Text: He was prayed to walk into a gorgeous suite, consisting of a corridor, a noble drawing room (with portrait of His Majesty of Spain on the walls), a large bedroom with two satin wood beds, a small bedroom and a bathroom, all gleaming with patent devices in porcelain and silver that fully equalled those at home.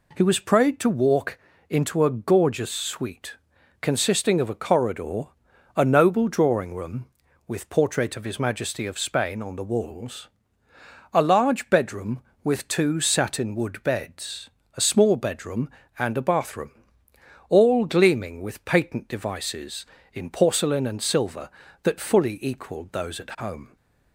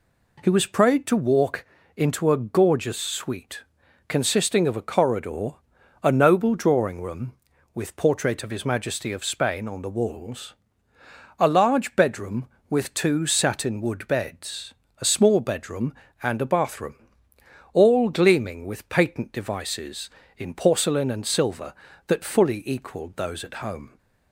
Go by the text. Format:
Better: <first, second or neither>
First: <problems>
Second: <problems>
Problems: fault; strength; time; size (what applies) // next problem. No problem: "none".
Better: neither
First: pauses between "walk" and "into"; slight; at 1.3 s; 0.32 s long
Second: pauses between "walk" and "into"; slight; at 1.6 s; 0.32 s long